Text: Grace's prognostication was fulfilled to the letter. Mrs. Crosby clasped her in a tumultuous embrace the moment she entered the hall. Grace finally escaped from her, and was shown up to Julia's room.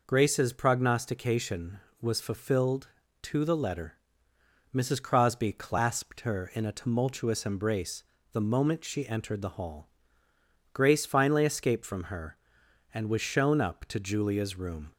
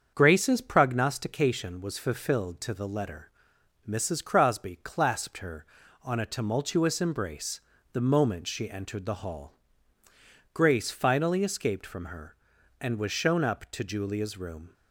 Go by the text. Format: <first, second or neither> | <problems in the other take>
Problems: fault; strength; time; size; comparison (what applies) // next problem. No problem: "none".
first | starts louder than the rest; strong; until 1.1 s; 7 dB // says "on" for "in"; at 6.0 s // pauses between "embrace" and "the"; slight; at 7.6 s; 0.32 s long; slight in the first